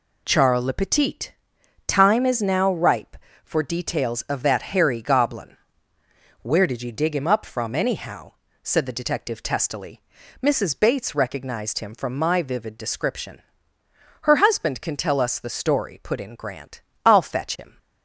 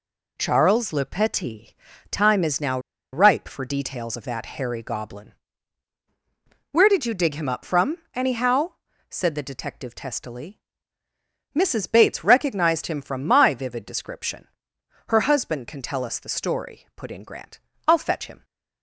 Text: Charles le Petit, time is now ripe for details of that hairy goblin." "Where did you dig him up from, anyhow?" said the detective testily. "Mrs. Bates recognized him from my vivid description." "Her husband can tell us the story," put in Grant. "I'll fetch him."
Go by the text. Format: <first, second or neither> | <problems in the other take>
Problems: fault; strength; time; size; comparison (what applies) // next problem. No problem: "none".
first | pauses between "now" and "ripe"; slight; at 2.7 s; 0.34 s long